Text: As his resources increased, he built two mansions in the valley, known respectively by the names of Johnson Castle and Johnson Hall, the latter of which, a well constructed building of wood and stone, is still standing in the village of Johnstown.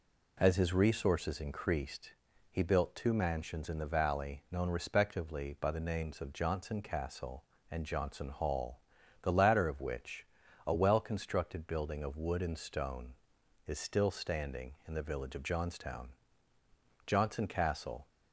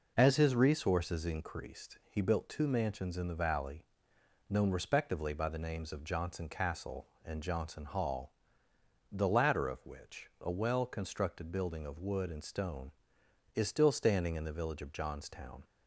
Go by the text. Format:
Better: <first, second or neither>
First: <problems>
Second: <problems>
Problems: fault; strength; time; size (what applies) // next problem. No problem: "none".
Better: second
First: goes on to say "Johnson Castle"; noticeable; from 17.0 s on; 1.0 s long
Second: none